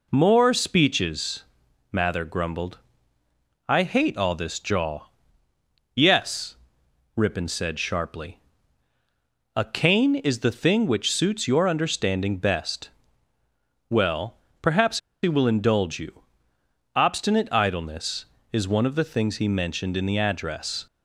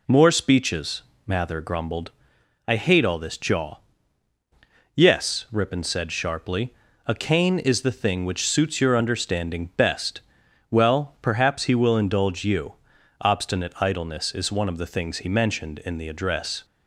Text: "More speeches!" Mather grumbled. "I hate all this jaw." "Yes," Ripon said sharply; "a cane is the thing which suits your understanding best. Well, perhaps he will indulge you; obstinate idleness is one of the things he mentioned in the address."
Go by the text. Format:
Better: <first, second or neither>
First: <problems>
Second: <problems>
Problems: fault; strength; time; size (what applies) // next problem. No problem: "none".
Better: second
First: pauses between "perhaps" and "he"; slight; at 14.9 s; 0.24 s long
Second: none